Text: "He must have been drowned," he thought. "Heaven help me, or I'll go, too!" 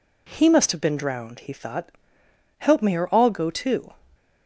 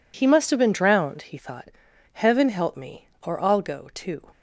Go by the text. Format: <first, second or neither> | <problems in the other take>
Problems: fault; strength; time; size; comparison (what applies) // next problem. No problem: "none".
second | skips "Heaven"; at 2.2 s